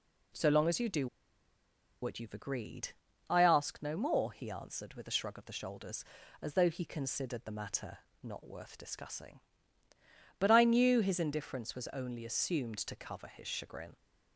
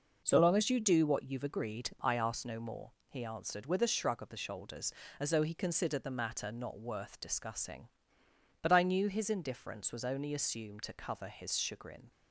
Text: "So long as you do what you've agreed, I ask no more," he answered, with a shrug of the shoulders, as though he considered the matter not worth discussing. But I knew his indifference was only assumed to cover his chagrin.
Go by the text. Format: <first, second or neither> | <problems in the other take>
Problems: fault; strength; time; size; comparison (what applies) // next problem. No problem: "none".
second | pauses between "do" and "what"; noticeable; at 1.0 s; 0.95 s long // pauses between "matter" and "not"; slight; at 7.9 s; 0.24 s long